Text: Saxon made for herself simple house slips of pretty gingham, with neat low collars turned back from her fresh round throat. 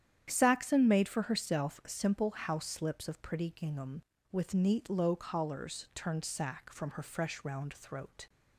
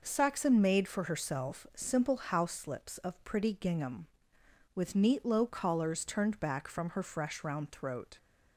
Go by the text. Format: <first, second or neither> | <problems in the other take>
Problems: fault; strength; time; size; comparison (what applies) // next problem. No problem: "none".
second | starts louder than the rest; strong; until 1.3 s; 9.5 dB // says "sack" for "back"; at 6.2 s